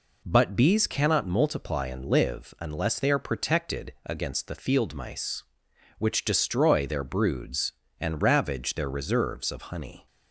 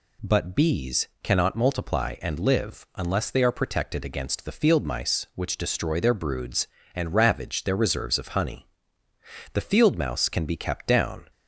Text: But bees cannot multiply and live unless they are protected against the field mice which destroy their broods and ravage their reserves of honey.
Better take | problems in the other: first | goes on to say "The field mouse can be kept down"; strong; from 9.5 s on; 1.7 s long

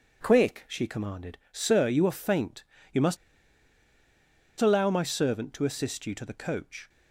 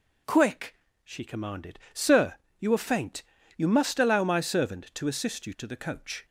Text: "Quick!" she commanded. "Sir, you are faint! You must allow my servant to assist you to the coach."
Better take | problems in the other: second | pauses between "must" and "allow"; strong; at 3.1 s; 1.4 s long

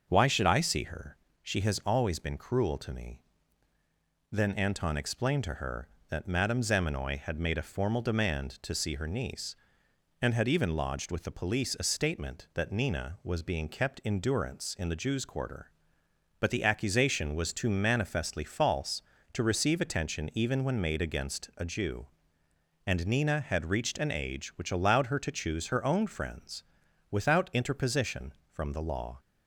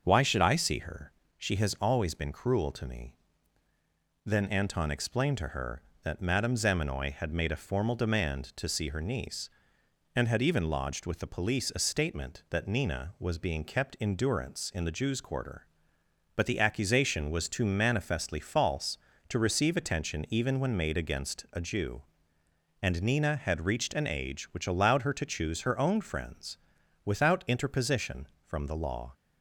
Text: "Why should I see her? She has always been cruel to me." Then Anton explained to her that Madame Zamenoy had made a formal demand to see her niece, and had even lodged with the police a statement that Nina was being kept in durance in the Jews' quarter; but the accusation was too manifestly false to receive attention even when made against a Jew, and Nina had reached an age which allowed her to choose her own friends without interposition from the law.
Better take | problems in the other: neither | starts louder than the rest; the same in both // pauses between "friends" and "without"; noticeable; the same in both

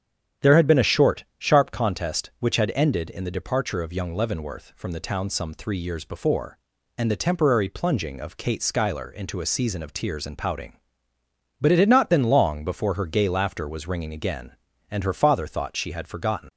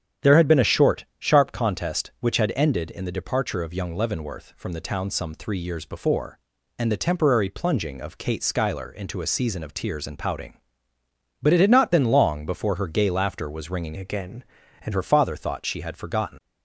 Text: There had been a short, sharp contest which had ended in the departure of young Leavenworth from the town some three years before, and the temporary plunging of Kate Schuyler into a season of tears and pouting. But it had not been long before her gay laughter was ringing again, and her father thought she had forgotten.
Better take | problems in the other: first | starts louder than the rest; strong; until 1.3 s; 9.5 dB; strong in the first // changes voice from "again" to "and"; from 13.9 to 14.9 s; 1.0 s long

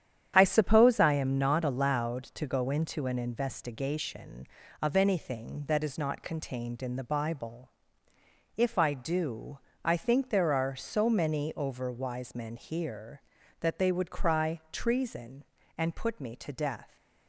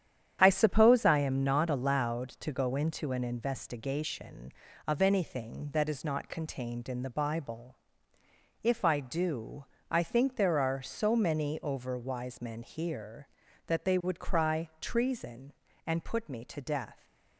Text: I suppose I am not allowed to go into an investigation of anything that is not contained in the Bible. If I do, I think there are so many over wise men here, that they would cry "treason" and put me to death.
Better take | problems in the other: neither | starts louder than the rest; strong; the same in both

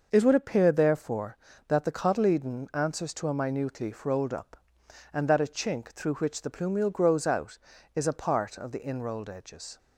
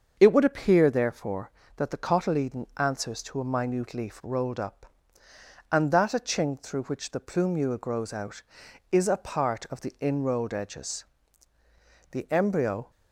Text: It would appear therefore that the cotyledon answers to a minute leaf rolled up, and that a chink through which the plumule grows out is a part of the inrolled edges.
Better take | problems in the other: first | starts louder than the rest; until 1.2 s; 6.5 dB // goes on to say "The embryo"; noticeable; from 12.1 s on; 0.78 s long

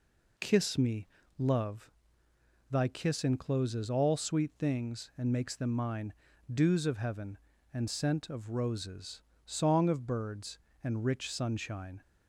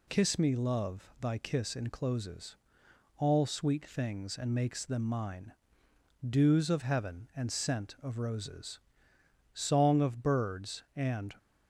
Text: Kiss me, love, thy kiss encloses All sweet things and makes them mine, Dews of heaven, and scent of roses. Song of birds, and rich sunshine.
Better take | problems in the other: first | pauses between "encloses" and "All"; noticeable; at 2.5 s; 0.64 s long // stops before "rich sunshine"; at 11.3 s

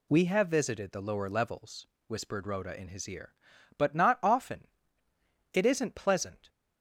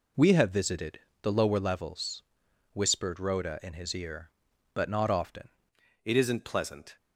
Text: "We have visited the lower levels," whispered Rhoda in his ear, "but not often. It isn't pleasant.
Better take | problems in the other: first | pauses between "visited" and "the"; slight; at 1.0 s; 0.22 s long // changes voice at "It"; from 6.0 s on; 0.9 s long

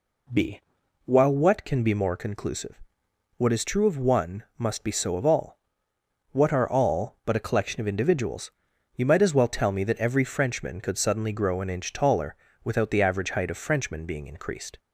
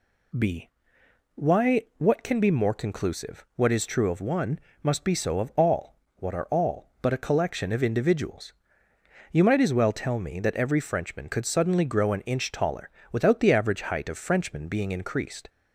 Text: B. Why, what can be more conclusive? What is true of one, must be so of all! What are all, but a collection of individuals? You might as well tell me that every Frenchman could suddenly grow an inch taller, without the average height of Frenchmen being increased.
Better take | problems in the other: second | says "While" for "Why"; at 1.0 s

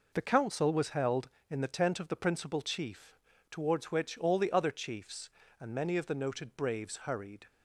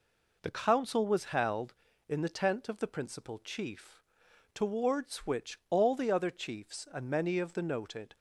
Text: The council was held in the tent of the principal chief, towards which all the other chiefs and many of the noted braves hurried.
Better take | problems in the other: first | stops before "braves hurried"; at 8.1 s

